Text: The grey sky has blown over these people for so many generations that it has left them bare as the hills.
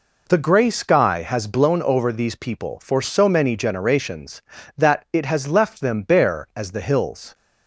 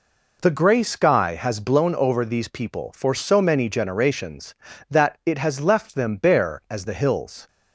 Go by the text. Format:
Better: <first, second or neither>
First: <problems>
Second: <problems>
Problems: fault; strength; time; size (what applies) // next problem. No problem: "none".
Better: neither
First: none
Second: none